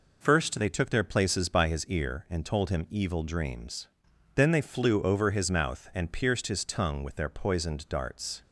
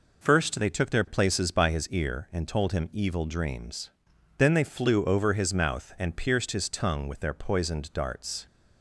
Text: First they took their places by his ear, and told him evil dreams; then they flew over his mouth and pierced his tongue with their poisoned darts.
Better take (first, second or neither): neither